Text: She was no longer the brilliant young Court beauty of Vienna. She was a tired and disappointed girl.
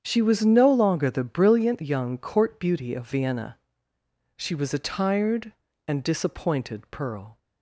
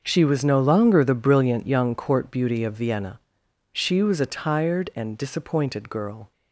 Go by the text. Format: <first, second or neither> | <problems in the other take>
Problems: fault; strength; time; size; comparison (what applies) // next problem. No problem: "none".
second | starts louder than the rest; strong; until 1.0 s; 8 dB; also in the second // says "pearl" for "girl"; at 6.9 s